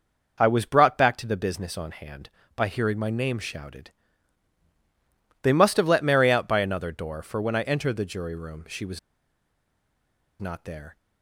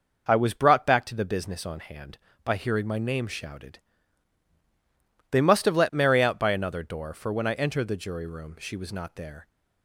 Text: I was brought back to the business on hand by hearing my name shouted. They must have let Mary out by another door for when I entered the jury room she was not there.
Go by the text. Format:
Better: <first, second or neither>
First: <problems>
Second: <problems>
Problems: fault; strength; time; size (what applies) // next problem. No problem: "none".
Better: second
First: pauses between "was" and "not"; strong; at 8.9 s; 1.4 s long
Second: none